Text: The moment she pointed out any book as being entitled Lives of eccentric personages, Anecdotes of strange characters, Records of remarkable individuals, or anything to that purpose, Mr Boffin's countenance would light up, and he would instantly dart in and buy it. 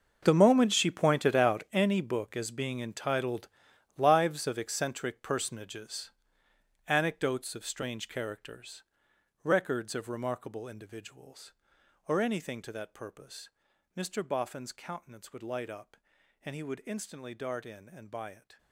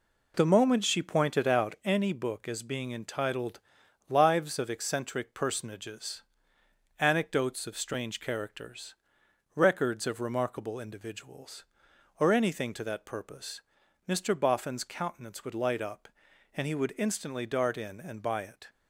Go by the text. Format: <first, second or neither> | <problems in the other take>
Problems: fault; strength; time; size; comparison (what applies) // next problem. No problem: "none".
second | gets quieter; strong; throughout; 16 dB // pauses between "entitled" and "Lives"; noticeable; at 3.4 s; 0.48 s long; noticeable in the second